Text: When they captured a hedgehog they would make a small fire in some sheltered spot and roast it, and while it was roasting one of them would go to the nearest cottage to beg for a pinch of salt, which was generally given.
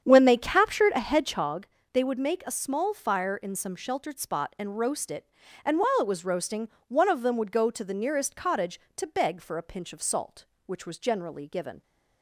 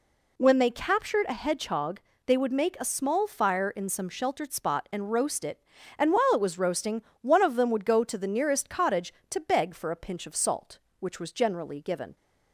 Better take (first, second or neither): second